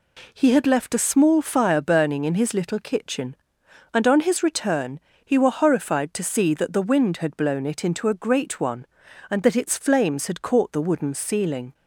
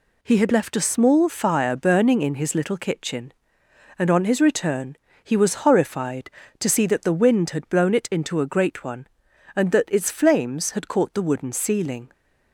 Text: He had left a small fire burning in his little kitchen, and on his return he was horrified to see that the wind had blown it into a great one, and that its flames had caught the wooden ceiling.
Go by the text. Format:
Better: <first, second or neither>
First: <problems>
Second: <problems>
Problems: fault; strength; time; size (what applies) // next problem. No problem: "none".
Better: second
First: pauses between "return" and "he"; slight; at 4.9 s; 0.24 s long // says "were" for "was"; at 5.3 s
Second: pauses between "return" and "he"; slight; at 4.9 s; 0.26 s long